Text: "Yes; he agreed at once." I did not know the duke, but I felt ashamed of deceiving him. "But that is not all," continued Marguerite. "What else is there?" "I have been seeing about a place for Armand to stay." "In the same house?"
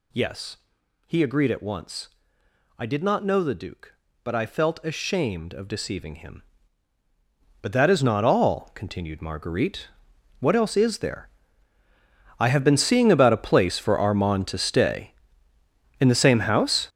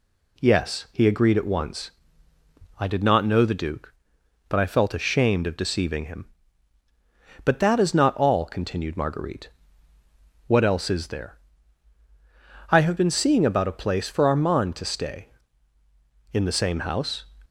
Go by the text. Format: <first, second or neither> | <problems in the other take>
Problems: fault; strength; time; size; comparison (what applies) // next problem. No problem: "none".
second | gets louder; strong; throughout; 12 dB